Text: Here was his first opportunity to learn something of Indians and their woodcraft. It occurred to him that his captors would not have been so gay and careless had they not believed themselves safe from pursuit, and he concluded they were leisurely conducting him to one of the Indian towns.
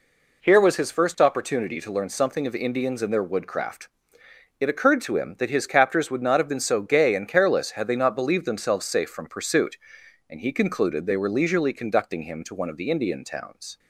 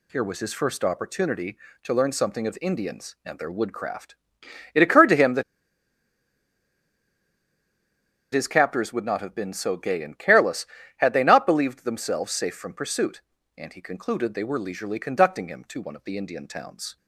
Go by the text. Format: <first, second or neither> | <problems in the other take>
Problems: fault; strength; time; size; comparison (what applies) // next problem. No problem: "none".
first | pauses between "that" and "his"; strong; at 5.4 s; 2.9 s long